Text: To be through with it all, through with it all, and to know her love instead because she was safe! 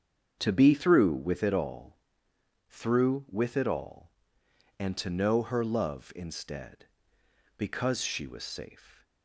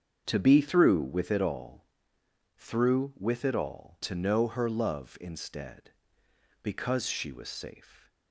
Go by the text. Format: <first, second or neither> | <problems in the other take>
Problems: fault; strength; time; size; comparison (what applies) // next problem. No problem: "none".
first | starts louder than the rest; strong; until 1.2 s; 7 dB; strong in the first // skips "and"; at 4.0 s